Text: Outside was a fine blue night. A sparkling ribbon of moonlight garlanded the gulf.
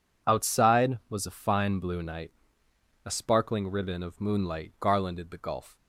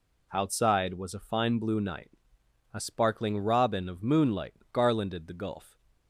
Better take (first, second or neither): first